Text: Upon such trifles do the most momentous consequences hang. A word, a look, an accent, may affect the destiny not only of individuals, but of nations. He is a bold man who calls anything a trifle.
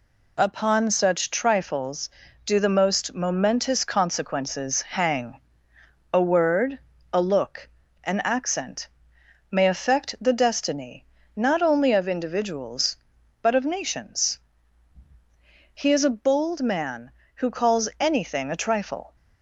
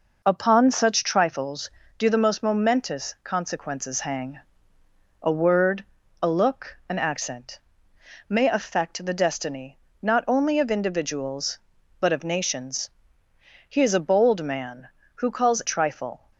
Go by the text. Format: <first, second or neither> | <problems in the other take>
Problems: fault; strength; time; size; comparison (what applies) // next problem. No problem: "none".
first | pauses between "destiny" and "not"; slight; at 9.8 s; 0.20 s long; slight in the first // skips "anything a"; at 15.6 s